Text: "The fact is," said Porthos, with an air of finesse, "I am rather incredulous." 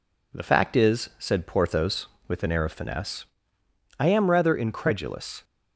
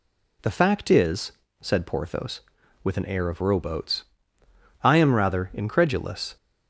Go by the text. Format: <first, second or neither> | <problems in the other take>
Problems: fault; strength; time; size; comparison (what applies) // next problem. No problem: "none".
first | says "rowboats" for "finesse"; at 3.4 s